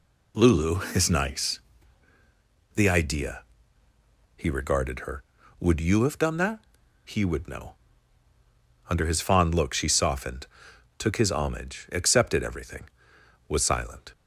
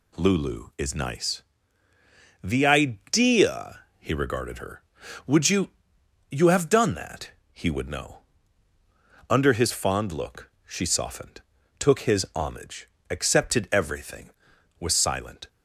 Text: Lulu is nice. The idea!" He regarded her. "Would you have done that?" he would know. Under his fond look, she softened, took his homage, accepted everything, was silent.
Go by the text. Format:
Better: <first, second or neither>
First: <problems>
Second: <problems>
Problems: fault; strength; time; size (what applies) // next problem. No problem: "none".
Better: first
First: none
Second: says "you" twice; at 6.2 s